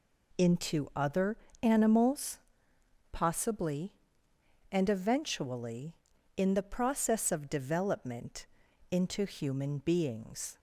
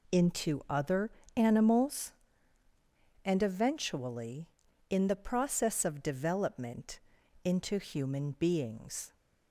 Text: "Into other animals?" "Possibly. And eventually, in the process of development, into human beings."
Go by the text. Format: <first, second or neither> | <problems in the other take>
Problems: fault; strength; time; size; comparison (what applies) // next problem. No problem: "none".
first | pauses between "other" and "animals"; slight; at 1.0 s; 0.26 s long; slight in the first // skips "Possibly"; at 2.6 s